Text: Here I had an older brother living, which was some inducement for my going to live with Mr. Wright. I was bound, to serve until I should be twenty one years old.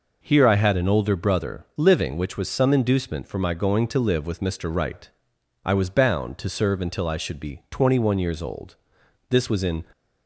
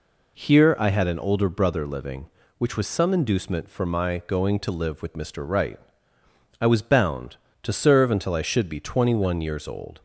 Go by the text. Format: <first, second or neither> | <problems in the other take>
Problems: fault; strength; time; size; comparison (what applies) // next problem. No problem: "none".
second | goes on to say "This was in"; from 9.3 s on; 0.52 s long